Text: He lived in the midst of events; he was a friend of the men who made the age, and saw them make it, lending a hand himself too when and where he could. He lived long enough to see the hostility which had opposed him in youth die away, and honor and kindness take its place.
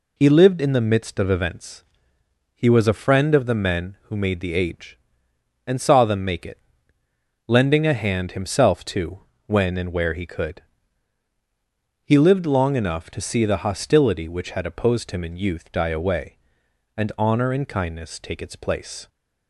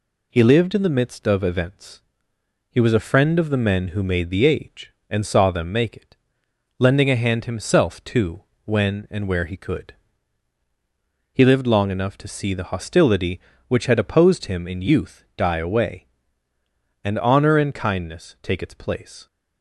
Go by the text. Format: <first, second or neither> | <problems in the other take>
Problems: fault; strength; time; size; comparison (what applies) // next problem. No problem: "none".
neither | pauses between "too" and "when"; slight; the same in both